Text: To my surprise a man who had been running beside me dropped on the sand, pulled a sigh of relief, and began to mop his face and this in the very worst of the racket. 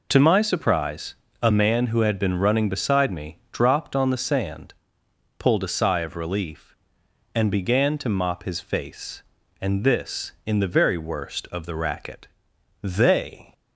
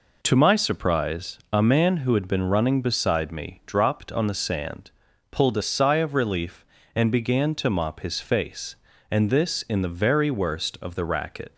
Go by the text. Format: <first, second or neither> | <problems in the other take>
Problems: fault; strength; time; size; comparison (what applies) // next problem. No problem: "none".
second | pauses between "surprise" and "a"; slight; at 1.1 s; 0.28 s long // goes on to say "They"; noticeable; from 12.8 s on; 0.70 s long